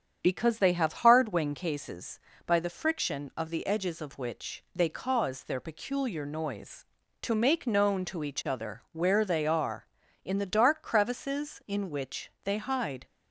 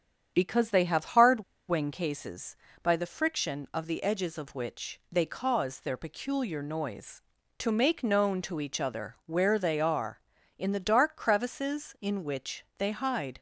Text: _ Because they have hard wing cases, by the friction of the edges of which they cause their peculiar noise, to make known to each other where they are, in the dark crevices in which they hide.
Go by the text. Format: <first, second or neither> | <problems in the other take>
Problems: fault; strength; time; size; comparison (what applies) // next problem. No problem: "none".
first | starts louder than the rest; strong; until 1.3 s; 8 dB; strong in the first // pauses between "hard" and "wing"; slight; at 1.4 s; 0.25 s long